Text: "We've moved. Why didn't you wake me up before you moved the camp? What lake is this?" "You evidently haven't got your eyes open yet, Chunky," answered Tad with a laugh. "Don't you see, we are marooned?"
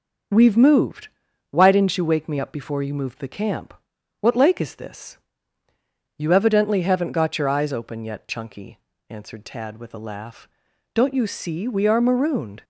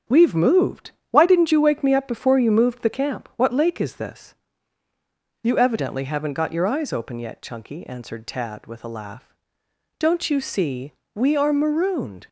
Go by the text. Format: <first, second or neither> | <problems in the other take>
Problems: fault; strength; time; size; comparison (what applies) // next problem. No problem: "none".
neither | starts louder than the rest; the same in both